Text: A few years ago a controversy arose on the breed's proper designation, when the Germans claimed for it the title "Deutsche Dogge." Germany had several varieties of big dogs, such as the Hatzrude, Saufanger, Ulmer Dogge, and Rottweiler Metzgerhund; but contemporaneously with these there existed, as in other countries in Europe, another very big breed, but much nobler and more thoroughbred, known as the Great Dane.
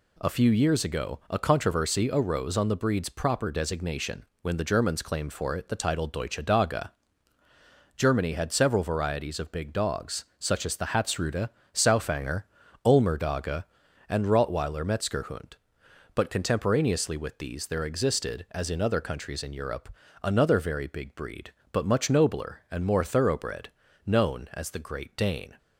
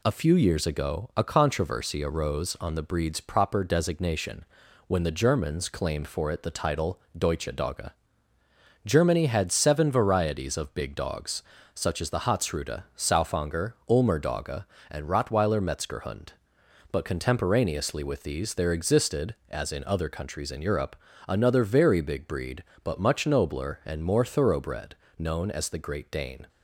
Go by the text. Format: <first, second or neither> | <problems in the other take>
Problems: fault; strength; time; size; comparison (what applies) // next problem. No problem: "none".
first | pauses between "title" and "Deutsche"; slight; at 6.9 s; 0.18 s long // says "seven" for "several"; at 9.5 s